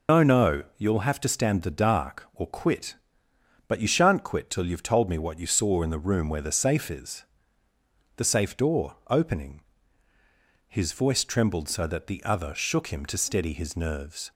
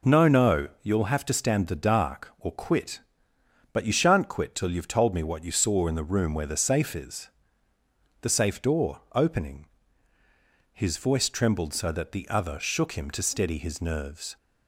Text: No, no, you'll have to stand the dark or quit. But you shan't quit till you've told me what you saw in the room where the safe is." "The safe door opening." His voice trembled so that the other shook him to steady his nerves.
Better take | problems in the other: second | loses the start of "No"; at 0.0 s; 110 ms

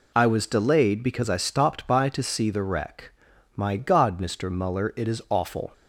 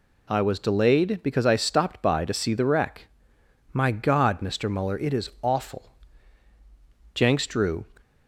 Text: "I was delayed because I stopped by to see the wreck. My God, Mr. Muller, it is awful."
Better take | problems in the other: first | goes on to say "Jenks drew"; noticeable; from 7.1 s on; 0.72 s long

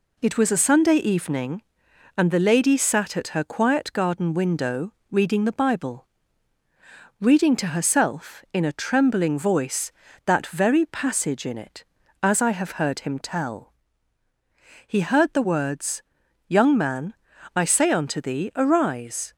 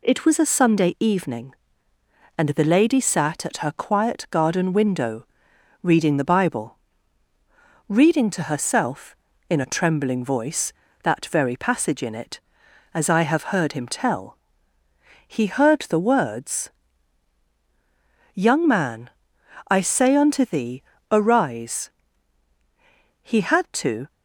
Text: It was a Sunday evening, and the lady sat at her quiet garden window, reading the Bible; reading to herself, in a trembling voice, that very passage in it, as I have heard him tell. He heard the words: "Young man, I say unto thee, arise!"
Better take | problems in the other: first | goes on to say "He had to"; noticeable; from 23.2 s on; 0.90 s long

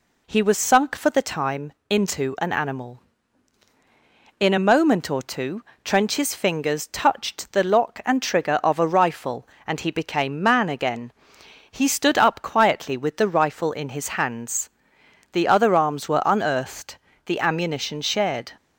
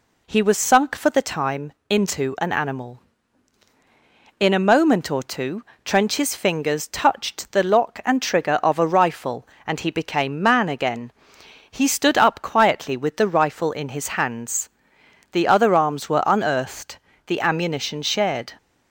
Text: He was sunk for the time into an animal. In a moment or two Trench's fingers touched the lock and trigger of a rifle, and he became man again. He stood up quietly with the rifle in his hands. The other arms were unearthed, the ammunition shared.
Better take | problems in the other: neither | pauses between "time" and "into"; slight; the same in both // pauses between "two" and "Trench's"; slight; the same in both

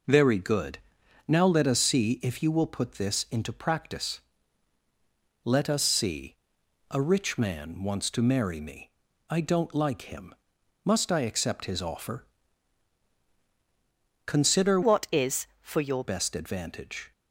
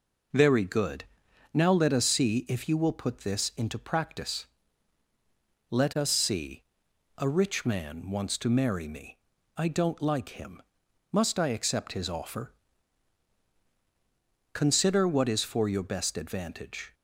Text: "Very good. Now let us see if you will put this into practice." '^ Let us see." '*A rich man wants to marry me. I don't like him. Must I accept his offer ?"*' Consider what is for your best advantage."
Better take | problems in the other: second | changes voice from "what" to "your"; from 14.8 to 16.0 s; 1.2 s long

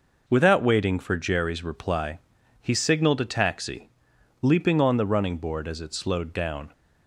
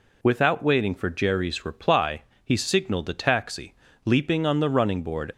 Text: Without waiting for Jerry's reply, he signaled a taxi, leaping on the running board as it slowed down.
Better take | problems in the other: first | stops before "as it slowed down"; at 5.3 s

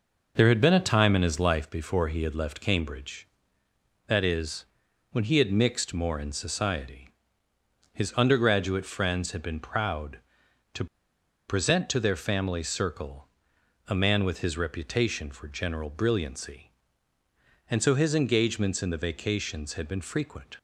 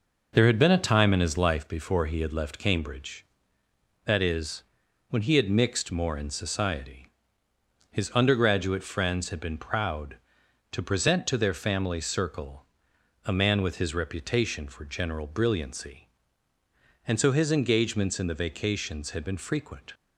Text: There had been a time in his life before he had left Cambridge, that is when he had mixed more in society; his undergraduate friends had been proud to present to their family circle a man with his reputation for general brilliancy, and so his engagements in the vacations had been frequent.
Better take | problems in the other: second | pauses between "is" and "when"; noticeable; at 4.6 s; 0.46 s long; noticeable in the second // pauses between "to" and "present"; noticeable; at 10.8 s; 0.62 s long // pauses between "circle" and "a"; noticeable; at 13.2 s; 0.58 s long; noticeable in the second

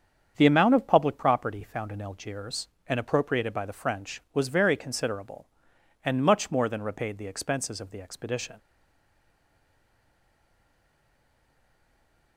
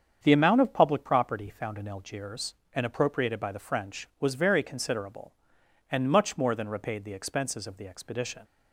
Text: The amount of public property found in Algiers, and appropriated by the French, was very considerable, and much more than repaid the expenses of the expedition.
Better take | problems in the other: second | starts louder than the rest; strong; until 1.3 s; 7.5 dB; strong in the second // stays silent after the last word; strong; from 8.5 s on; 3.8 s long

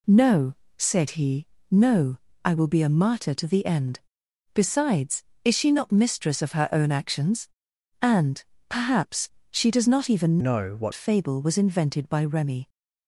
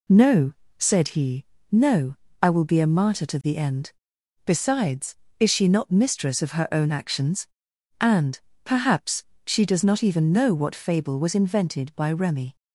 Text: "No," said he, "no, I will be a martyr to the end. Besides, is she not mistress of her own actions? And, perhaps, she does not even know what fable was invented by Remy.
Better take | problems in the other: second | changes voice from "know" to "what"; from 10.4 to 10.9 s; 0.5 s long

